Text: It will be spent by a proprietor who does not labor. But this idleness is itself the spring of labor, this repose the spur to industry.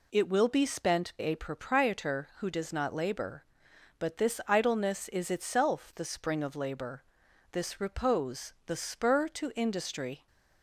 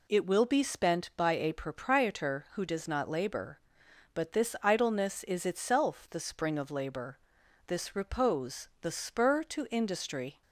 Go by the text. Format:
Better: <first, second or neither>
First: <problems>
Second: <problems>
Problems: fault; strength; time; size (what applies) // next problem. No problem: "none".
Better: second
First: skips "by"; at 1.1 s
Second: none